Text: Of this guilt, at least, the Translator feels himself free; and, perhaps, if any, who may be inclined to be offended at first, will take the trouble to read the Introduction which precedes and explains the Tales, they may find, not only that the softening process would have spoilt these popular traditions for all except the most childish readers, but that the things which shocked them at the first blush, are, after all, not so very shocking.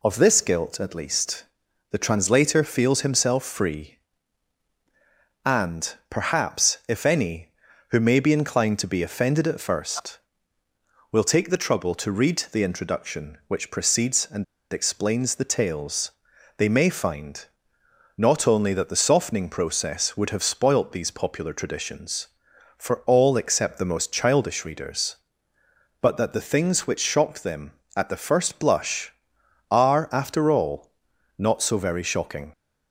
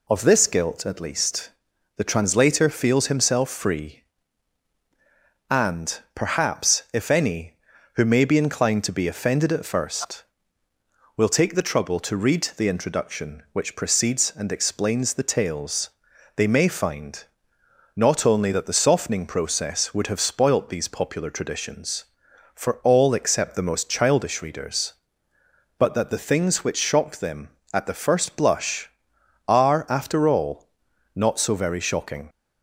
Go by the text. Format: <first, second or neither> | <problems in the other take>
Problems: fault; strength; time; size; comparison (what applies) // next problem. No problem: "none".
second | pauses between "and" and "explains"; slight; at 14.4 s; 0.29 s long